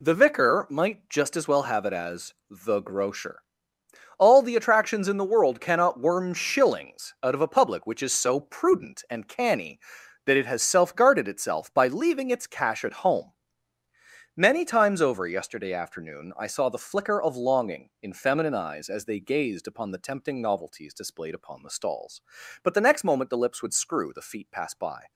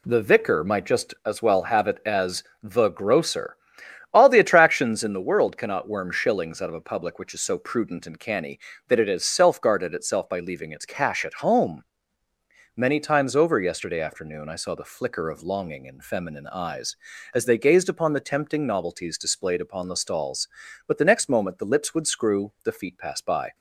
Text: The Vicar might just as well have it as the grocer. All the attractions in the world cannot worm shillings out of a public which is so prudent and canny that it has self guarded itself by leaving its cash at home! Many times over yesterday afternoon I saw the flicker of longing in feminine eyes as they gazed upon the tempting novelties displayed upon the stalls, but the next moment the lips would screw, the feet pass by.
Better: neither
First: pauses between "as" and "the"; slight; at 2.3 s; 0.16 s long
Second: pauses between "as" and "the"; slight; at 2.4 s; 0.20 s long

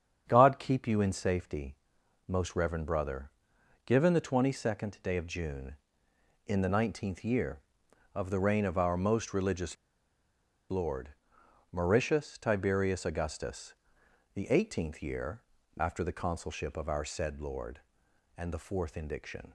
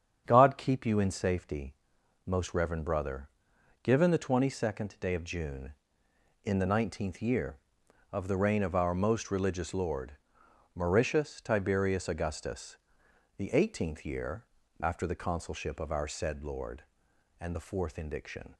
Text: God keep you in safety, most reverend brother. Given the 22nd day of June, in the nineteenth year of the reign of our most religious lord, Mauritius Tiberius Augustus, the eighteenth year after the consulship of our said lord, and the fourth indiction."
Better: second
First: starts louder than the rest; strong; until 1.2 s; 7.5 dB // pauses between "religious" and "lord"; noticeable; at 9.7 s; 0.94 s long // pauses between "year" and "after"; slight; at 15.4 s; 0.36 s long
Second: starts louder than the rest; strong; until 1.2 s; 7.5 dB // pauses between "year" and "after"; slight; at 14.4 s; 0.36 s long

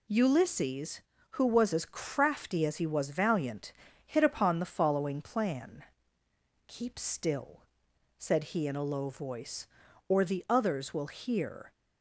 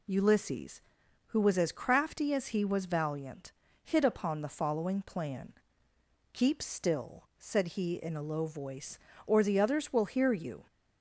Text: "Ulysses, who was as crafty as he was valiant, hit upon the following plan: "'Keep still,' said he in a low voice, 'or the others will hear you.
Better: second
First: stops before "you"; at 11.7 s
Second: none

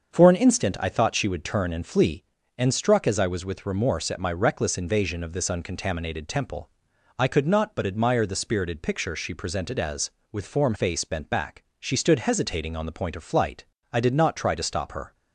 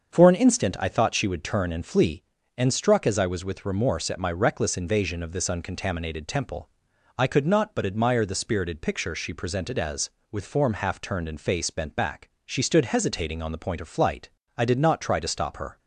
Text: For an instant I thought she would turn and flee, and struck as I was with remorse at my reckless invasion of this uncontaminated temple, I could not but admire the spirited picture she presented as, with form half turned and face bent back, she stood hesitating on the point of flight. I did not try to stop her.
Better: second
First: starts louder than the rest; until 1.1 s; 6.5 dB // skips "half turned and"; at 10.7 s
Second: starts louder than the rest; until 1.1 s; 6.5 dB

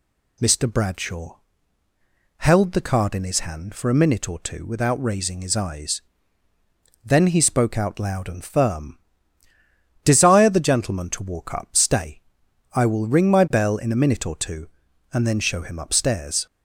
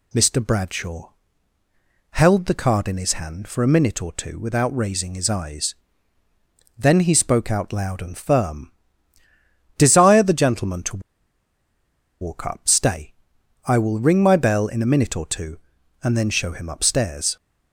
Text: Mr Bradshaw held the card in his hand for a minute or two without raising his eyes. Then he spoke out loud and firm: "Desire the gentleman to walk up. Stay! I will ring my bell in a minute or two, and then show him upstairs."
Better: first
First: pauses between "Bradshaw" and "held"; at 1.3 s; 1.0 s long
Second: pauses between "Bradshaw" and "held"; at 1.1 s; 1.0 s long // pauses between "to" and "walk"; at 11.0 s; 1.2 s long

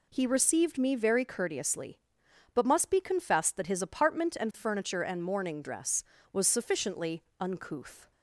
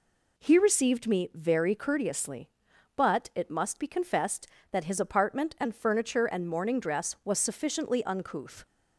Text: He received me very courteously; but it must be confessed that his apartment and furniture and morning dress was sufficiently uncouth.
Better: second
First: skips "it"; at 2.6 s // pauses between "sufficiently" and "uncouth"; slight; at 7.2 s; 0.16 s long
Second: none

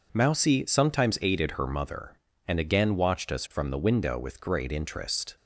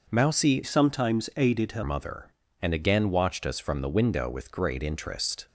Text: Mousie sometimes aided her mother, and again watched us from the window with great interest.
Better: first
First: none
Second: changes voice from "sometimes" to "her"; from 0.6 to 1.8 s; 1.2 s long

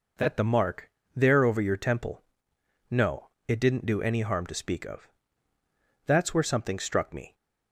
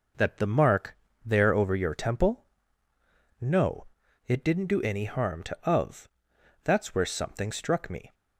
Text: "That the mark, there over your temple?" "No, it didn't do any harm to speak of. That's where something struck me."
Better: first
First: none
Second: skips "speak"; at 5.6 s

